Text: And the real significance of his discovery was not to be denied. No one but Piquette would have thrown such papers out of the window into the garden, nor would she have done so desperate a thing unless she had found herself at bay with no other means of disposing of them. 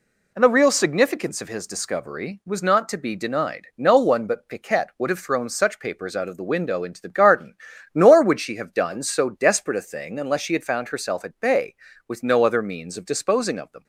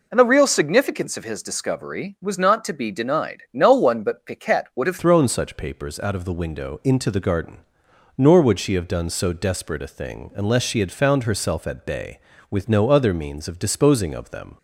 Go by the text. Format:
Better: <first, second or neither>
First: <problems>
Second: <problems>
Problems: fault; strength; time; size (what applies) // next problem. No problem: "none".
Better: first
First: none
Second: changes voice at "thrown"; from 4.9 s on; 9.6 s long